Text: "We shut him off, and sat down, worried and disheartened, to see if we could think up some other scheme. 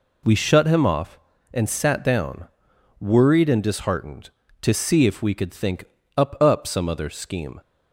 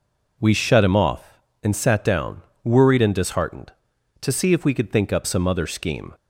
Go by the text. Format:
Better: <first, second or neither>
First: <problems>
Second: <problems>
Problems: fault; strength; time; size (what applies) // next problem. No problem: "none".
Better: second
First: pauses between "think" and "up"; slight; at 5.8 s; 0.32 s long // says "up" twice; at 6.4 s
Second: none